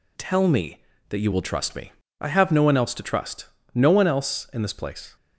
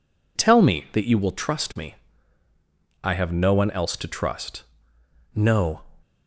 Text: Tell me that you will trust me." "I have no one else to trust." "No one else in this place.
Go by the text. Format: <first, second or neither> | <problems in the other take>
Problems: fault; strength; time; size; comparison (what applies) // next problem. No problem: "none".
first | stops before "one else in this place"; at 6.0 s